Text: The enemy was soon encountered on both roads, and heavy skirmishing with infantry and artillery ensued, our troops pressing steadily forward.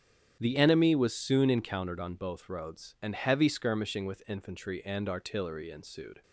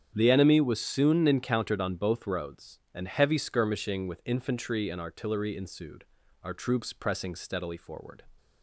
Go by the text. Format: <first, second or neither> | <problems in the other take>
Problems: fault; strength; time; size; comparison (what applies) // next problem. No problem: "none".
second | starts louder than the rest; strong; until 1.4 s; 9.5 dB; strong in the second // stops before "our troops pressing steadily forward"; at 6.2 s